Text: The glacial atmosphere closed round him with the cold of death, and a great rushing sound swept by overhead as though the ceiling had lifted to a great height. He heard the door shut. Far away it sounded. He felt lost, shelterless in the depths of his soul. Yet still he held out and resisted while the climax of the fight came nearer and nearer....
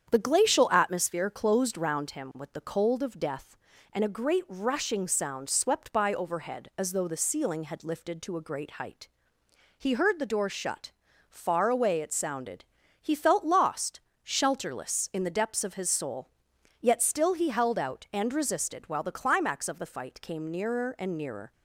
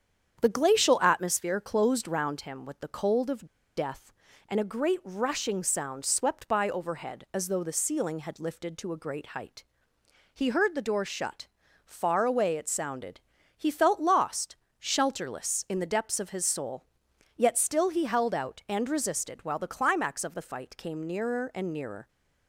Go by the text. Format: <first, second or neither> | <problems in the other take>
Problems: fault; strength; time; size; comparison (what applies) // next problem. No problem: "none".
first | starts louder than the rest; strong; until 1.4 s; 8 dB; strong in the first // pauses between "of" and "death"; slight; at 3.4 s; 0.31 s long